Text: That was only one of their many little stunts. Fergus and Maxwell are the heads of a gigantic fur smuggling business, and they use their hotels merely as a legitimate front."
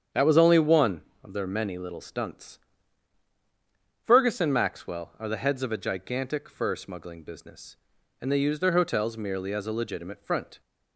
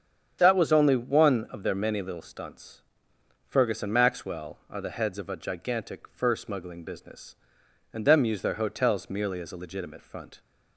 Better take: first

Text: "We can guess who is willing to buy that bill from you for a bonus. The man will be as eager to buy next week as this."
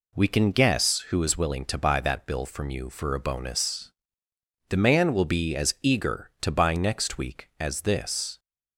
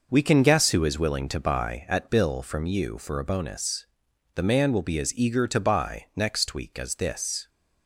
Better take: first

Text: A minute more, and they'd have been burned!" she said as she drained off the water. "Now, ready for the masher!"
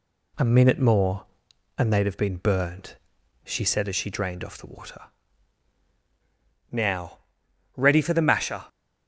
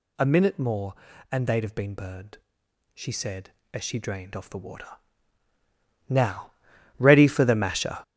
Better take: first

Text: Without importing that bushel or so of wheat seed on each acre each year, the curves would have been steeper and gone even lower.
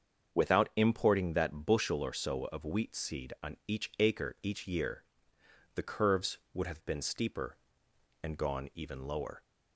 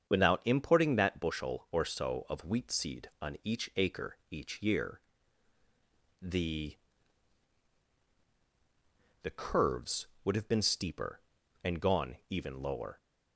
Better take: first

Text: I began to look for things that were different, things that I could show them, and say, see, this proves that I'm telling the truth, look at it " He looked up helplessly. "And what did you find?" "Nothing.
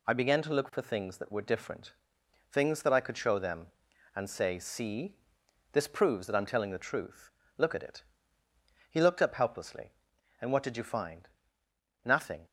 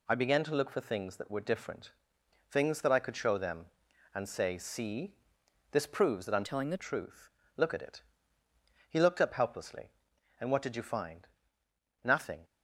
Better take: first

